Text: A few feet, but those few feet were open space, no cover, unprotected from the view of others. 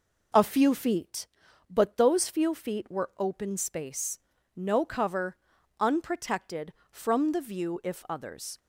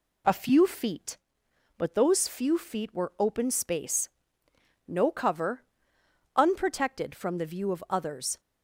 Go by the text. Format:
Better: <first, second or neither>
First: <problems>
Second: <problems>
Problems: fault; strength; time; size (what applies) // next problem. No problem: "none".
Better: second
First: says "if" for "of"; at 7.8 s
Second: none